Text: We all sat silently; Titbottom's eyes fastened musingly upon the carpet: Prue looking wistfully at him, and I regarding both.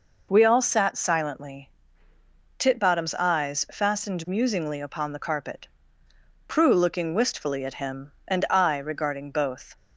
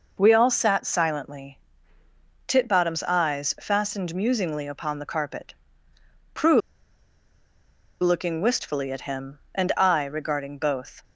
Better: first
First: none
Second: pauses between "Prue" and "looking"; strong; at 6.6 s; 1.4 s long

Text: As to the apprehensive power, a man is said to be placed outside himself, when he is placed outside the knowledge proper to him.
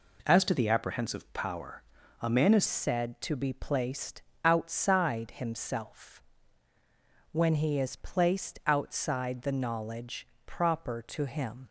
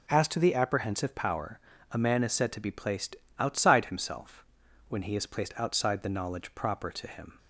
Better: second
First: changes voice at "said"; from 2.6 s on; 9.0 s long // pauses between "placed" and "outside"; slight; at 4.2 s; 0.24 s long // pauses between "knowledge" and "proper"; slight; at 10.2 s; 0.18 s long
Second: pauses between "placed" and "outside"; slight; at 3.1 s; 0.24 s long

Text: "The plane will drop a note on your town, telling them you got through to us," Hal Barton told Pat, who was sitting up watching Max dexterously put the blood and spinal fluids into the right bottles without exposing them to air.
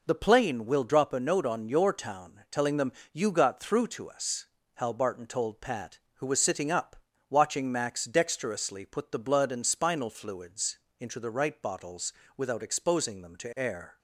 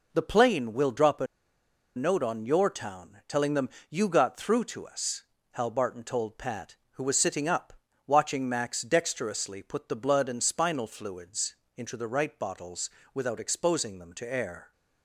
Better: first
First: pauses between "them" and "you"; slight; at 2.9 s; 0.22 s long // pauses between "up" and "watching"; slight; at 6.9 s; 0.34 s long // pauses between "fluids" and "into"; slight; at 10.7 s; 0.22 s long // pauses between "bottles" and "without"; slight; at 12.1 s; 0.24 s long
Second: pauses between "a" and "note"; noticeable; at 1.2 s; 0.71 s long // pauses between "them" and "you"; slight; at 3.6 s; 0.22 s long // pauses between "up" and "watching"; slight; at 7.7 s; 0.34 s long // pauses between "fluids" and "into"; slight; at 11.5 s; 0.22 s long // pauses between "bottles" and "without"; slight; at 12.8 s; 0.24 s long

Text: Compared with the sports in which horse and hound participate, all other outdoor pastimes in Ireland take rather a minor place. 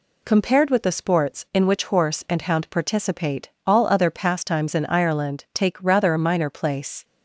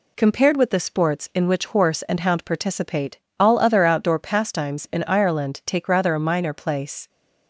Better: second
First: skips "outdoor"; at 4.1 s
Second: none

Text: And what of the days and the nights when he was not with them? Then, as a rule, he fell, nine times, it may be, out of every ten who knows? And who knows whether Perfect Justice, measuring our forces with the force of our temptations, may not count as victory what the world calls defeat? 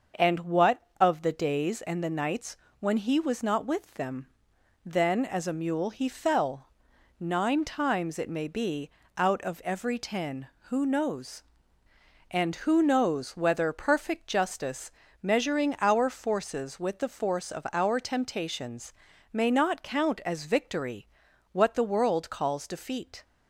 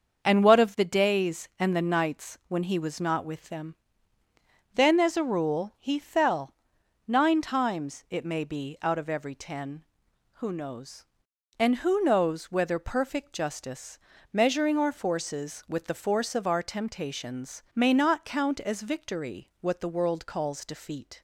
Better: second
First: starts louder than the rest; until 1.3 s; 6.5 dB // pauses between "nights" and "when"; slight; at 2.5 s; 0.23 s long // says "mule" for "rule"; at 5.5 s // pauses between "victory" and "what"; at 21.0 s; 0.44 s long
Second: starts louder than the rest; until 1.2 s; 6.5 dB

